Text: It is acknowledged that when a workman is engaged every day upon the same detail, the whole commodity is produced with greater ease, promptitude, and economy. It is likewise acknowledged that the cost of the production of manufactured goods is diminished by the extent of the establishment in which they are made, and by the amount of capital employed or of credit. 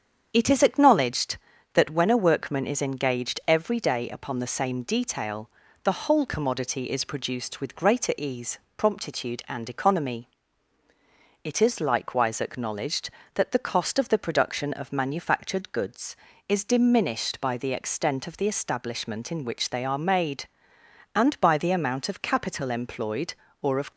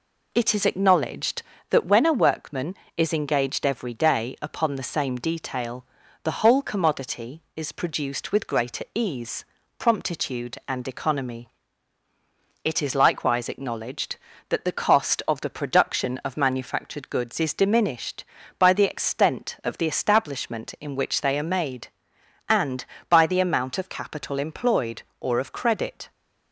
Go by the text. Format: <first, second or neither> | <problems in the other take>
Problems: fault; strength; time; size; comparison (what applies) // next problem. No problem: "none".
second | starts louder than the rest; strong; until 1.3 s; 7.5 dB // stops before "credit"; at 23.9 s